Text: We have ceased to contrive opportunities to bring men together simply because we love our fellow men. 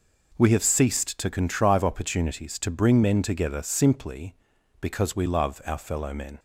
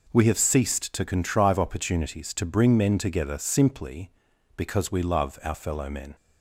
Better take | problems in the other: neither | none

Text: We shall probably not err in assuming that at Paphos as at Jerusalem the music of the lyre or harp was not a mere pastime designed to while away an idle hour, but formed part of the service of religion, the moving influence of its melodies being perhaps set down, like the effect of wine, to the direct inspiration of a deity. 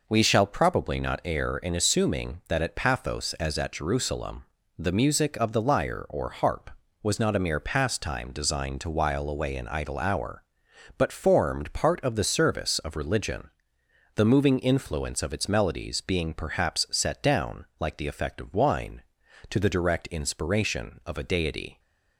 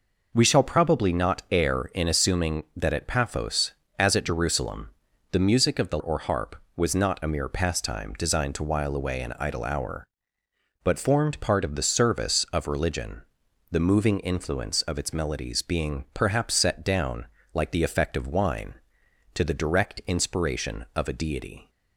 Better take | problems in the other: first | pauses between "Jerusalem" and "the"; at 4.9 s; 0.40 s long; slight in the first // skips "lyre"; at 5.9 s

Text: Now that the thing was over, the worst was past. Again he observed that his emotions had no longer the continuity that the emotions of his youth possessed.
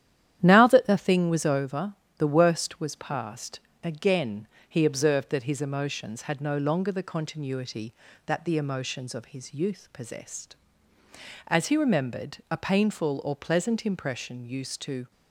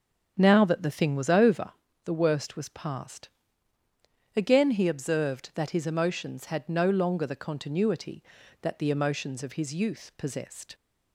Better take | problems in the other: second | starts louder than the rest; strong; until 1.4 s; 11 dB; strong in the second // pauses between "Again" and "he"; slight; at 4.4 s; 0.24 s long // goes on to say "As he remembered a painful or pleasant impression used to"; strong; from 11.4 s on; 3.6 s long

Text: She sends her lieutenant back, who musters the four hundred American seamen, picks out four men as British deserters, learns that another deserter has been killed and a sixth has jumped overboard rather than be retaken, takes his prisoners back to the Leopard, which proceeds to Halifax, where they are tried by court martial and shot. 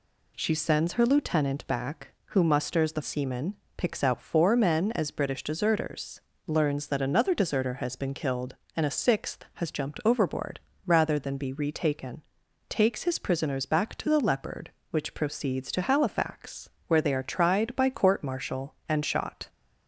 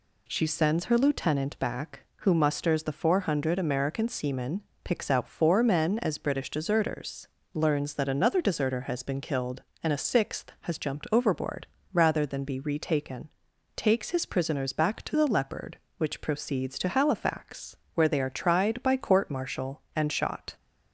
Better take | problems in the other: second | skips "four hundred American"; at 3.0 s // pauses between "overboard" and "rather"; slight; at 10.6 s; 0.26 s long; slight in the second

